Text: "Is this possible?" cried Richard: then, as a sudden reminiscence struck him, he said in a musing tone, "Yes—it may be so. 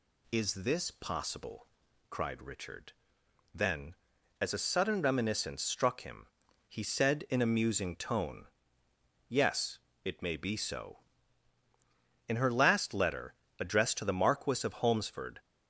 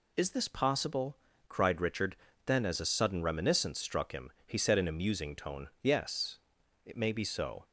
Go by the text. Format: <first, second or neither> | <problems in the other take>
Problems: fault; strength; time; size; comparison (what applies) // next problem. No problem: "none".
second | goes on to say "In her last letter addressed to the Marquis of Holmesford"; strong; from 12.2 s on; 3.1 s long